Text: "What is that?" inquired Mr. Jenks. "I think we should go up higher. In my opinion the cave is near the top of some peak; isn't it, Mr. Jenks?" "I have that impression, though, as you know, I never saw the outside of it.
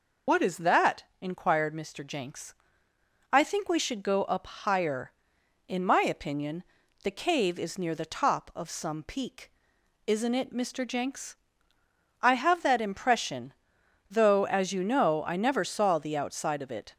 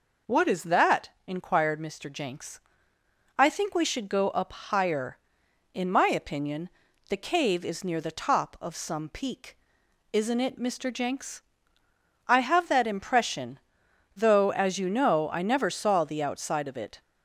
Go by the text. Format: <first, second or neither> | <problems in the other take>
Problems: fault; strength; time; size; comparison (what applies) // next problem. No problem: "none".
second | loses the start of "What"; at 0.2 s; 65 ms // pauses between "opinion" and "the"; at 6.6 s; 0.40 s long; also in the second